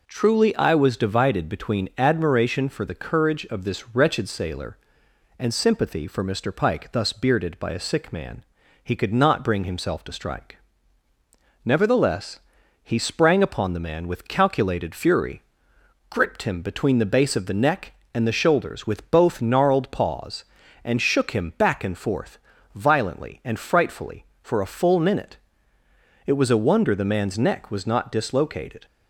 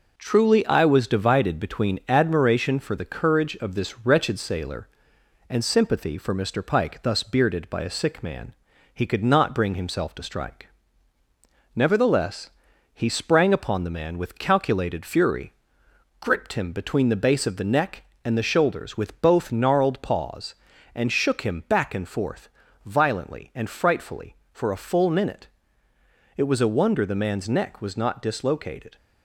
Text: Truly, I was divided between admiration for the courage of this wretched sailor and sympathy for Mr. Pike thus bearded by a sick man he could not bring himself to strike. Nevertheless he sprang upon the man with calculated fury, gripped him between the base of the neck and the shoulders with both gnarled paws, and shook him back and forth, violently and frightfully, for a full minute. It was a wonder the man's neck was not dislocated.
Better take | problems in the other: first | gets quieter; throughout; 3.5 dB // pauses between "man" and "he"; at 8.5 s; 0.40 s long; also in the first // pauses between "Nevertheless" and "he"; at 12.4 s; 0.44 s long; also in the first

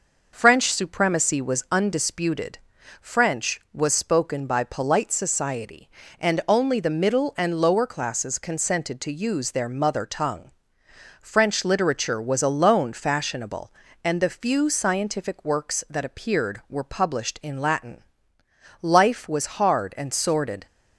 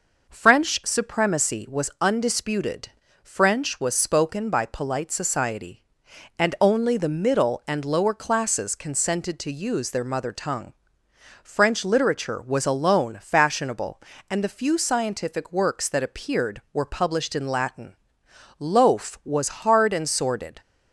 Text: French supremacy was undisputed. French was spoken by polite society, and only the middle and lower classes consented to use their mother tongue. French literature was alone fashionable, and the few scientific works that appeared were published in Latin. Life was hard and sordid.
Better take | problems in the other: first | says "Loaf" for "Life"; at 18.5 s

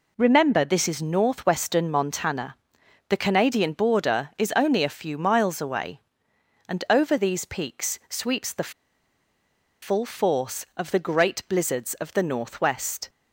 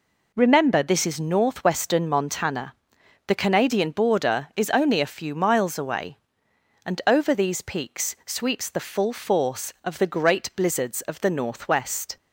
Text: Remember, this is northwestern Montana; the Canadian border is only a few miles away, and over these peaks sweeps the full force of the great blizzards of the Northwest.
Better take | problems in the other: second | pauses between "the" and "full"; at 8.7 s; 1.1 s long

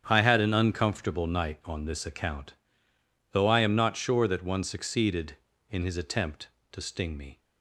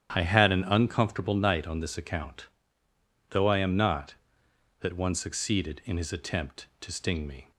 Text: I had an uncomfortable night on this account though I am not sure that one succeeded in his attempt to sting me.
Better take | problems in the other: first | starts louder than the rest; strong; until 1.1 s; 10 dB; strong in the first // pauses between "account" and "though"; noticeable; at 2.4 s; 0.82 s long; noticeable in the first // skips "sure"; at 4.4 s

